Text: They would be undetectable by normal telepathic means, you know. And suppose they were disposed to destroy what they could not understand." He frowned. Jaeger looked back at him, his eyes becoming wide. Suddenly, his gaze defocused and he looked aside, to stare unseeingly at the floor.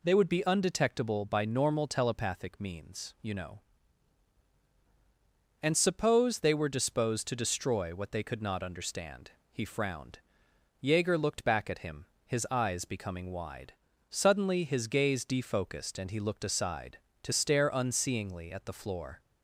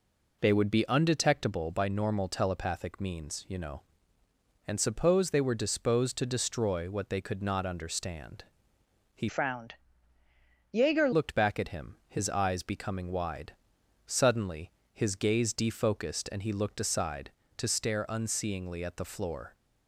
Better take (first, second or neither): first